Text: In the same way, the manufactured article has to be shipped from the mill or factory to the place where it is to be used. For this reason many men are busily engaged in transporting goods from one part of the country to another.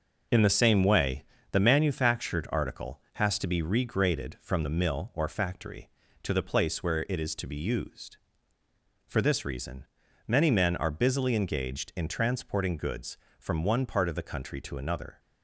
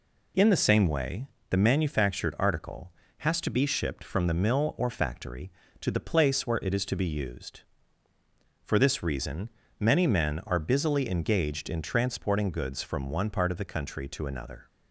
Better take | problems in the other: second | says "regraded" for "shipped"; at 3.6 s // pauses between "reason" and "many"; at 9.8 s; 0.40 s long; slight in the second

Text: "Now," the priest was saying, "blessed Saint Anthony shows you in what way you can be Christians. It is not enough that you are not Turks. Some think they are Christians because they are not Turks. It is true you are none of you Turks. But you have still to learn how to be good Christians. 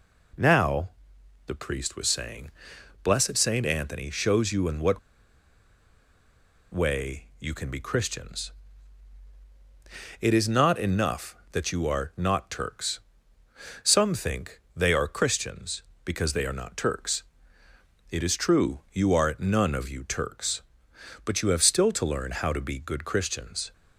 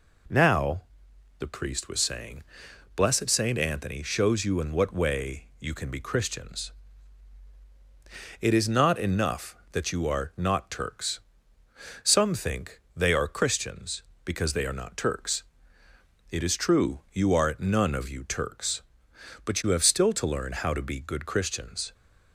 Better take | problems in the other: second | pauses between "what" and "way"; strong; at 4.9 s; 1.7 s long

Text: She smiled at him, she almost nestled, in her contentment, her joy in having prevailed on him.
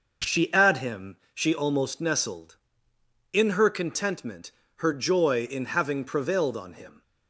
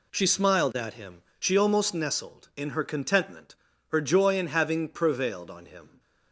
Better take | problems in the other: second | skips "smiled"; at 0.5 s

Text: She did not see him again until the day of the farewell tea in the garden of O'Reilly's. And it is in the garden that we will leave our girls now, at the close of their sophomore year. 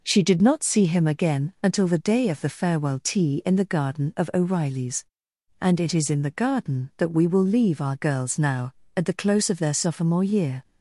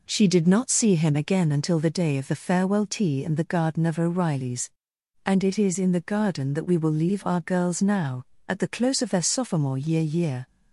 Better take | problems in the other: first | says "year" twice; at 10.0 s

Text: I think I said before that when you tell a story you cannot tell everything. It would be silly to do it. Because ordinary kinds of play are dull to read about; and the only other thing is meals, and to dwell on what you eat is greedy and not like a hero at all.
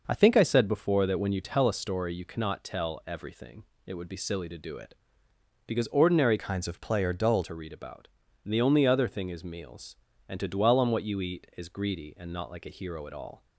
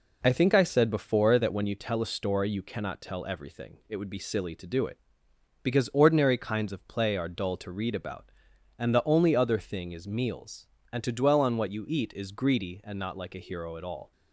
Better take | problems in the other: second | changes voice from "kinds" to "dull"; from 6.3 to 7.4 s; 1.1 s long

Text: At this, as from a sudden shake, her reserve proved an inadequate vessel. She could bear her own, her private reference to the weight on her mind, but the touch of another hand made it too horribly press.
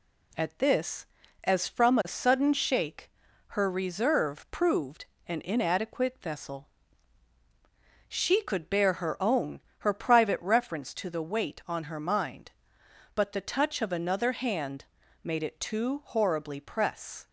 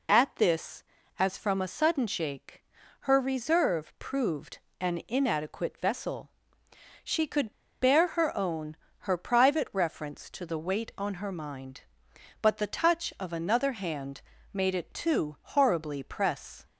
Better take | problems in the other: first | pauses between "proved" and "an"; slight; at 4.5 s; 0.22 s long; slight in the first // pauses between "could" and "bear"; slight; at 7.5 s; 0.29 s long // pauses between "hand" and "made"; slight; at 14.2 s; 0.32 s long; also in the first

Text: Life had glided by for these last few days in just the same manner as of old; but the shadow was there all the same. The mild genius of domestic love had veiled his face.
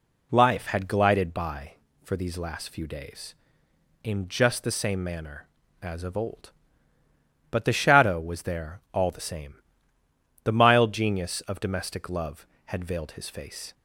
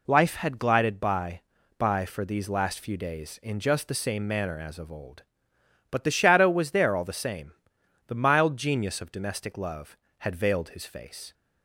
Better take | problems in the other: first | says "by" twice; at 1.7 s

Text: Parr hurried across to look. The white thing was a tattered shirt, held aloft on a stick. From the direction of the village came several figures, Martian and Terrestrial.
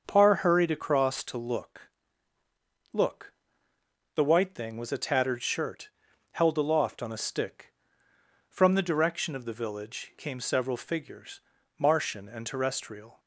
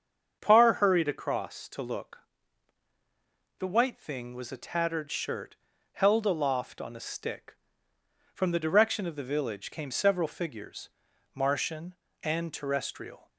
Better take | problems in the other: second | starts louder than the rest; until 1.0 s; 6.5 dB; strong in the second // says "look" twice; at 2.9 s

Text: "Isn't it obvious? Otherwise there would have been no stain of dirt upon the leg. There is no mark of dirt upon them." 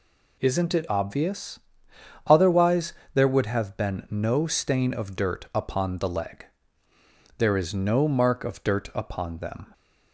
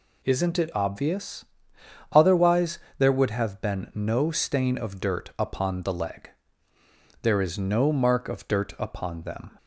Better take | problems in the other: neither | pauses between "Otherwise" and "there"; slight; the same in both

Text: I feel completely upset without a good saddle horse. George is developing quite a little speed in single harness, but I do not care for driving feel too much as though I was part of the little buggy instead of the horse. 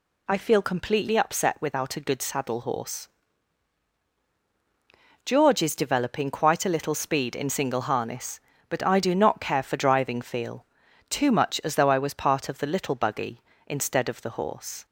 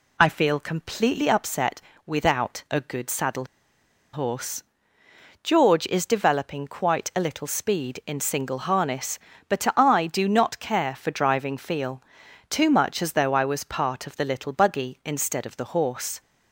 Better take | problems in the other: first | pauses between "upset" and "without"; slight; at 1.7 s; 0.28 s long // pauses between "saddle" and "horse"; noticeable; at 3.4 s; 0.67 s long // pauses between "feel" and "too"; noticeable; at 12.0 s; 0.48 s long; also in the first

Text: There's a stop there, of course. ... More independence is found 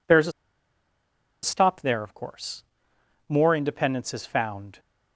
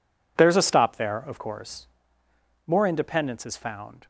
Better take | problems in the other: second | pauses between "a" and "stop"; at 0.3 s; 1.1 s long

